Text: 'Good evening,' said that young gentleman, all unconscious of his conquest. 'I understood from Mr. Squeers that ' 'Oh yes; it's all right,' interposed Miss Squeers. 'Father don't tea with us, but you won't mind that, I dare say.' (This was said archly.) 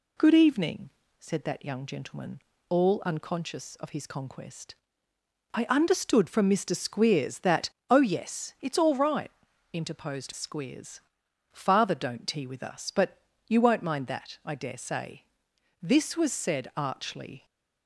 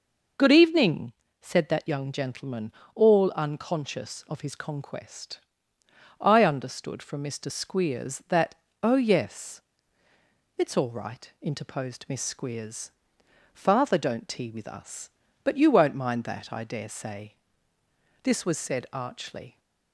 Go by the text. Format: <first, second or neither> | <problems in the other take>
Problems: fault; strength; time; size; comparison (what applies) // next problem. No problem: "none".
second | skips "Miss"; at 10.3 s // pauses between "but" and "you"; slight; at 13.2 s; 0.26 s long